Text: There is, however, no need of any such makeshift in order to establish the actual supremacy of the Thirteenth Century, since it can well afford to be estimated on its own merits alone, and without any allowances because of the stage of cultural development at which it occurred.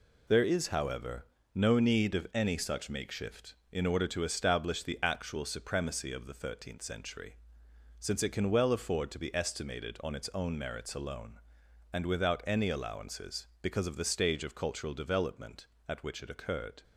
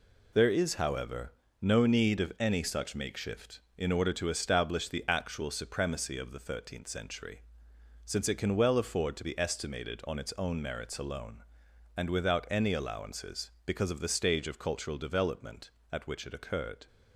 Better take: neither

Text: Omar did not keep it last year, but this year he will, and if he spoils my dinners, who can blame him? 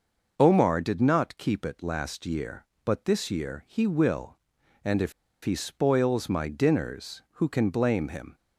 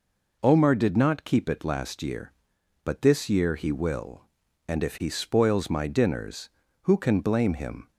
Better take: second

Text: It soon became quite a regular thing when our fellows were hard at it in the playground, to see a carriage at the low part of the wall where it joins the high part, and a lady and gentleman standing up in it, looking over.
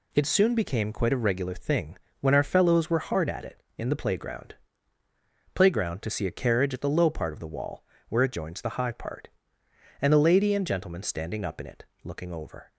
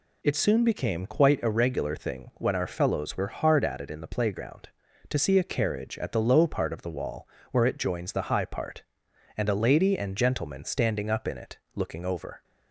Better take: second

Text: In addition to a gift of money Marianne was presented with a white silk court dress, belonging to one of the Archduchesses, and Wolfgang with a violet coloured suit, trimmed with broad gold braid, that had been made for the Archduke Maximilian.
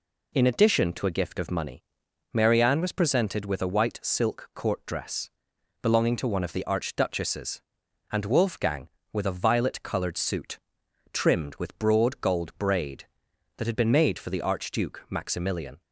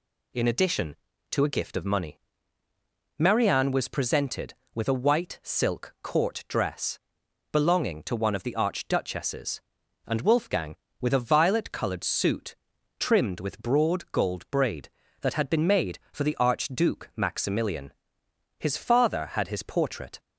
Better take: first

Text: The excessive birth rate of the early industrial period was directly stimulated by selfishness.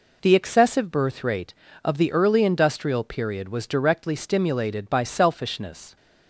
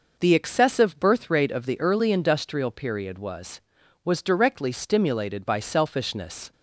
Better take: first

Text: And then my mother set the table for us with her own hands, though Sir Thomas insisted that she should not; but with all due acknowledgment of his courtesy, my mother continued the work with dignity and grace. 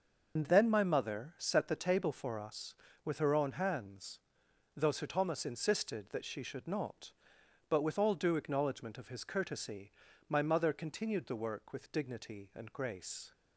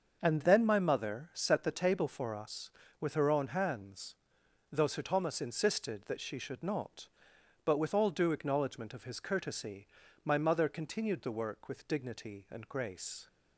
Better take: second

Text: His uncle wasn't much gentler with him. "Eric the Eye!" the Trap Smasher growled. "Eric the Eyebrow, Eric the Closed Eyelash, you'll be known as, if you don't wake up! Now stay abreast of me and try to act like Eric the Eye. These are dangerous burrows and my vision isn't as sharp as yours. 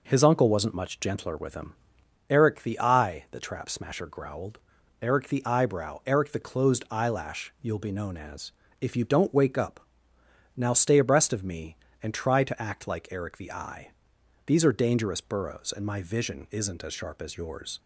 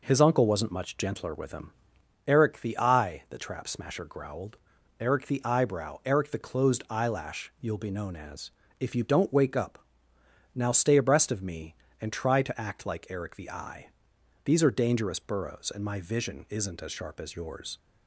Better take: neither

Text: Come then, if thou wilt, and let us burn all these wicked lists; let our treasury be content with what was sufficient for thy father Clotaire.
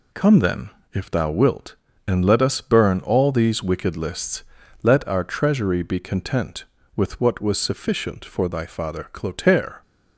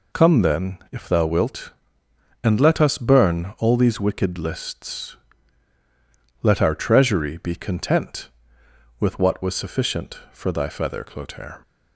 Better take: first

